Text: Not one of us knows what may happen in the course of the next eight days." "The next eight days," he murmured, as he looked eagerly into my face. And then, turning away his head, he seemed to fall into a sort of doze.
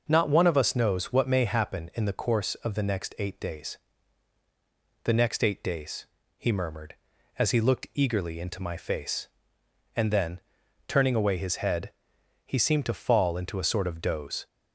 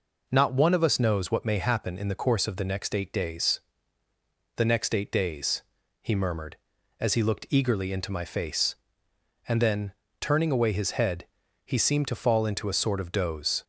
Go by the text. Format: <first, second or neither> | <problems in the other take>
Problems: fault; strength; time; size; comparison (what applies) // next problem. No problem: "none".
neither | none